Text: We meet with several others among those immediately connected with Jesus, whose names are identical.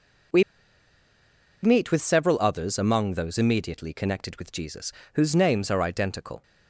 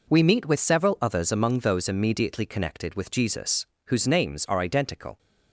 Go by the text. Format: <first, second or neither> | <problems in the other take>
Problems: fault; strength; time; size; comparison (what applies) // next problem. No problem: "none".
second | pauses between "We" and "meet"; at 0.4 s; 1.2 s long